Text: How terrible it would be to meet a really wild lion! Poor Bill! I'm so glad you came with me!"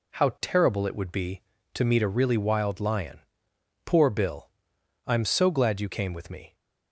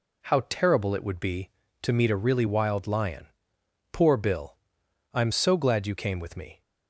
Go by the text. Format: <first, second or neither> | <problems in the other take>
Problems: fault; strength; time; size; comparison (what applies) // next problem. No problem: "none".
neither | none